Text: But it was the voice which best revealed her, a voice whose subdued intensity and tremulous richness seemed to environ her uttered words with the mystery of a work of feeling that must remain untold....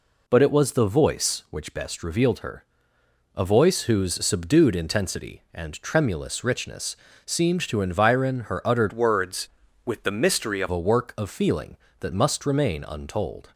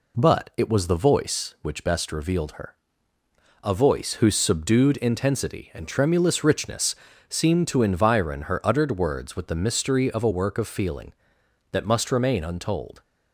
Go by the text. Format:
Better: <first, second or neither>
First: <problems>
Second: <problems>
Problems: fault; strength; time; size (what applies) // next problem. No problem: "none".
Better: second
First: pauses between "richness" and "seemed"; slight; at 6.9 s; 0.28 s long // changes voice from "words" to "of"; from 8.9 to 10.6 s; 1.7 s long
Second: pauses between "richness" and "seemed"; slight; at 6.9 s; 0.34 s long